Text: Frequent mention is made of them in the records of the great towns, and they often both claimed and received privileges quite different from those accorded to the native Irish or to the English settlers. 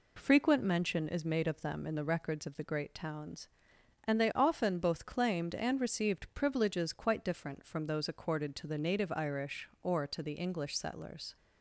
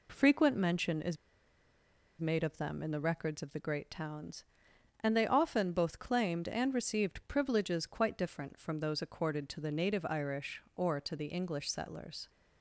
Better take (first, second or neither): first